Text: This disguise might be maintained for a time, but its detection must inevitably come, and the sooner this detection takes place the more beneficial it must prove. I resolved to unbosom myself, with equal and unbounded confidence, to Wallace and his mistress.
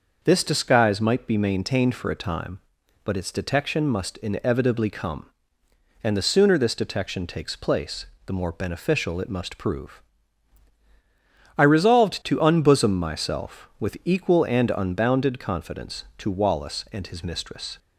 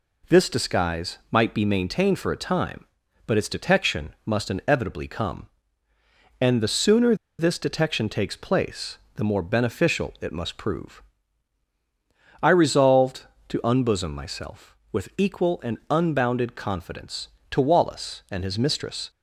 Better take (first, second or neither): first